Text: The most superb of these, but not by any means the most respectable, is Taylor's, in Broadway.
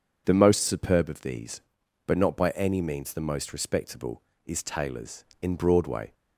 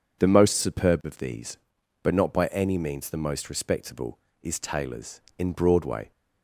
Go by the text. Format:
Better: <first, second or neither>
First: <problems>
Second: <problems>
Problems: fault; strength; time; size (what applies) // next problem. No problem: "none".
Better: neither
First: none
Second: none